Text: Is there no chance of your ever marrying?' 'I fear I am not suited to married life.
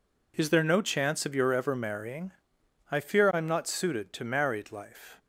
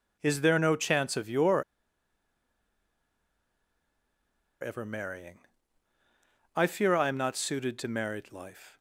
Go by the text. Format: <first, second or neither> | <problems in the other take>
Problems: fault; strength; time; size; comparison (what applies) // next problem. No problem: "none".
first | pauses between "your" and "ever"; strong; at 1.6 s; 2.9 s long